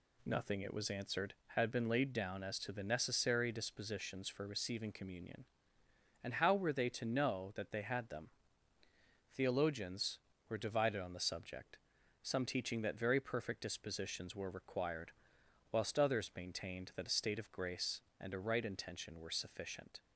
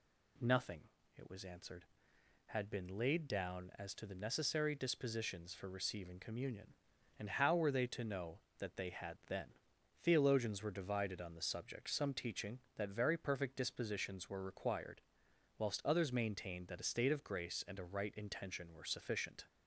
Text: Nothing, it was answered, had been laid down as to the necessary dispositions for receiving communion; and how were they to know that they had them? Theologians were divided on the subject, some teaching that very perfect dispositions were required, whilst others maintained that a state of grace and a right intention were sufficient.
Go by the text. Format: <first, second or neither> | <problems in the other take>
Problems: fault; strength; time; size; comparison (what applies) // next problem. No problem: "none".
first | says "then" for "them"; at 9.2 s